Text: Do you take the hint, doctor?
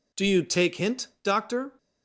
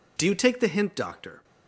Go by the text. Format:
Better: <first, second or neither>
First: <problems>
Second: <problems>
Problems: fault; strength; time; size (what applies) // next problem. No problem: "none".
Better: second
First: skips "the"; at 0.7 s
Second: none